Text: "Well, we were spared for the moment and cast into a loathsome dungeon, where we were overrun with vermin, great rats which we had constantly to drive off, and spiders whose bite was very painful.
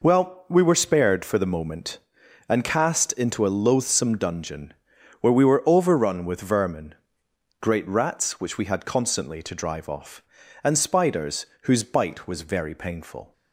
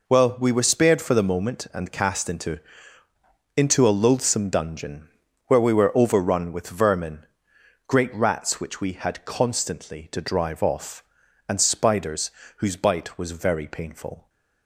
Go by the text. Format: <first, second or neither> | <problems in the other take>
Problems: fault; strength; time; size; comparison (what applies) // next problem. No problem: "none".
first | says "into" twice; at 3.5 s // pauses between "spiders" and "whose"; slight; at 12.2 s; 0.28 s long; slight in the first